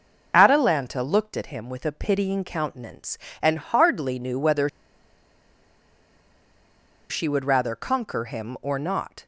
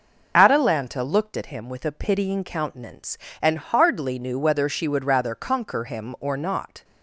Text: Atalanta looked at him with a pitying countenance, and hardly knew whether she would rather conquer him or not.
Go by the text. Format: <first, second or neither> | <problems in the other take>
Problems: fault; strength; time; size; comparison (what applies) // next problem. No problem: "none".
second | pauses between "whether" and "she"; strong; at 4.6 s; 2.4 s long